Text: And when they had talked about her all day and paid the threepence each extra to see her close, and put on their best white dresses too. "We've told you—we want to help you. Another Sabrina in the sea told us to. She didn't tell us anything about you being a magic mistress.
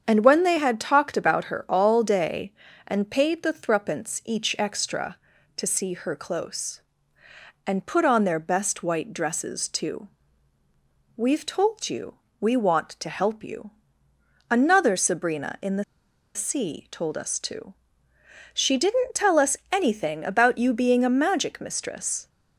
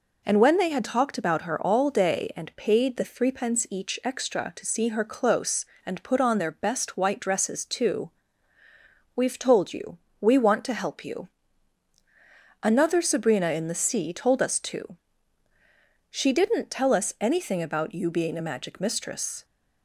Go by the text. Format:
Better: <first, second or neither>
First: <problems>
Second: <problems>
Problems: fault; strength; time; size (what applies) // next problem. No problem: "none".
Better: second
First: starts louder than the rest; strong; until 1.0 s; 7.5 dB // pauses between "the" and "sea"; noticeable; at 15.8 s; 0.51 s long // pauses between "us" and "anything"; slight; at 19.5 s; 0.16 s long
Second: none